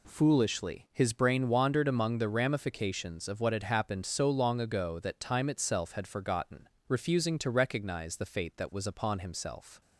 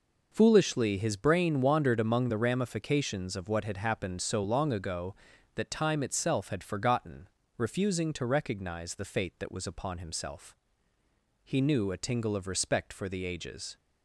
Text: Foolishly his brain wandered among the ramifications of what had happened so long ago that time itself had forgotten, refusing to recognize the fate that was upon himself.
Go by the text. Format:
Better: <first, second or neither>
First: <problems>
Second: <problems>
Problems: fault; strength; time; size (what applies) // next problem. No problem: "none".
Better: first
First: none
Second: goes on to say "He knew a tingle of respect for the ages"; strong; from 11.4 s on; 2.3 s long